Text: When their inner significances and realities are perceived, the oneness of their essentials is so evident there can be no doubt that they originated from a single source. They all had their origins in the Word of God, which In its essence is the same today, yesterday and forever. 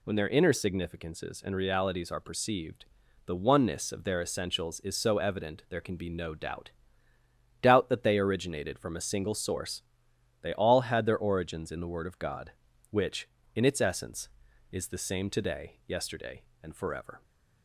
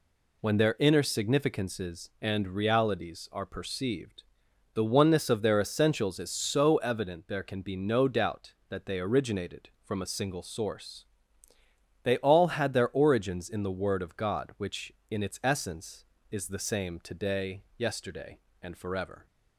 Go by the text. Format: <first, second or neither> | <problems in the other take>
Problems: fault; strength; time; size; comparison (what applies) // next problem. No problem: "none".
second | says "doubt" twice; at 7.6 s